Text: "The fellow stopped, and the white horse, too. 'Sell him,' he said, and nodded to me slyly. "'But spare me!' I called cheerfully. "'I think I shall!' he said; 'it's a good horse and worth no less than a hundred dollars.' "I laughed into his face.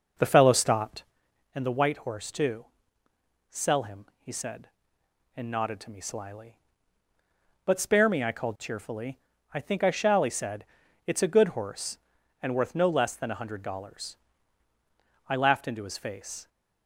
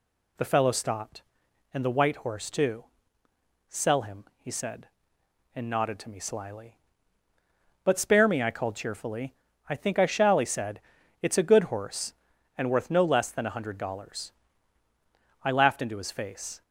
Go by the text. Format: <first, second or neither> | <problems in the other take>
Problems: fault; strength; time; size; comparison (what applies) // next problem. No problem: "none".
second | starts louder than the rest; noticeable; until 1.2 s; 5.5 dB